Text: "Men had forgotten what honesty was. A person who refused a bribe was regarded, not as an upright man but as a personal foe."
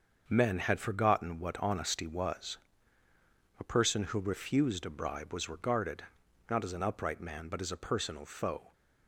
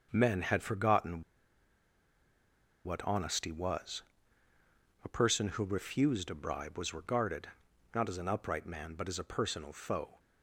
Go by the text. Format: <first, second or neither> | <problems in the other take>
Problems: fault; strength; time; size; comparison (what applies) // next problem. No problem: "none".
first | starts louder than the rest; until 1.1 s; 6.5 dB; also in the first // pauses between "forgotten" and "what"; strong; at 1.2 s; 1.6 s long